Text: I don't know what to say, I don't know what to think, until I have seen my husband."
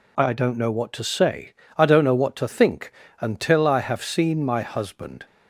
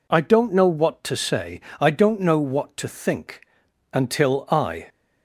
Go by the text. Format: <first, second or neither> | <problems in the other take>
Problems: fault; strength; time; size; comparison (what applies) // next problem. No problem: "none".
first | stops before "have seen my husband"; at 4.8 s